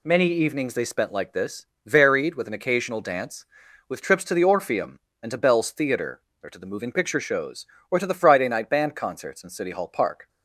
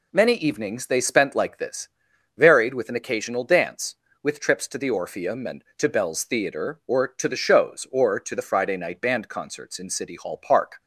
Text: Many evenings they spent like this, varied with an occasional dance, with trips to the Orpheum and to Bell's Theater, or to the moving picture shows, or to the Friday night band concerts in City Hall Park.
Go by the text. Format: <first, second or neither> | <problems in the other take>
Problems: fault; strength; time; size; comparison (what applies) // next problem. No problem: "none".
first | skips "moving picture"; at 7.3 s